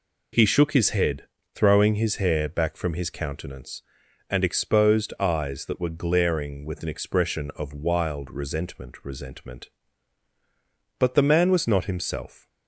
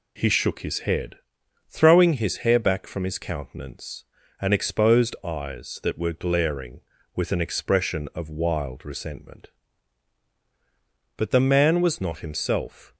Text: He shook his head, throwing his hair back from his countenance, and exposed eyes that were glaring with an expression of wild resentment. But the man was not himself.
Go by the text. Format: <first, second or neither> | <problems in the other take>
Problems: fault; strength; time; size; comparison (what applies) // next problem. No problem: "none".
second | says "resentment" twice; at 9.0 s